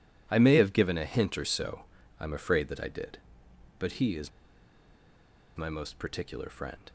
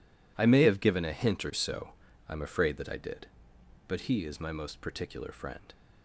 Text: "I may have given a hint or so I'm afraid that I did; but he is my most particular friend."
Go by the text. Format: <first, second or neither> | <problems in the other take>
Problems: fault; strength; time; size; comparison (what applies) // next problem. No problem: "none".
second | pauses between "so" and "I'm"; slight; at 1.8 s; 0.34 s long; slight in the second // pauses between "is" and "my"; strong; at 4.2 s; 1.2 s long